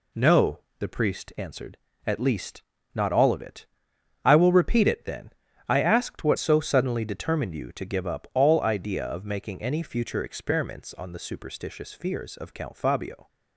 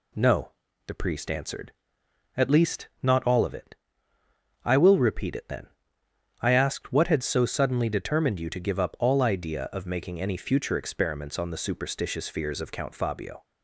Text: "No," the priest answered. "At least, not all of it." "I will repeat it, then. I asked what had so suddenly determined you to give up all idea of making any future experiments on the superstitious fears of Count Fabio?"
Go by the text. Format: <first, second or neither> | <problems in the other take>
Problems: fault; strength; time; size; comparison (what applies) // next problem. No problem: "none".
second | skips "had"; at 6.3 s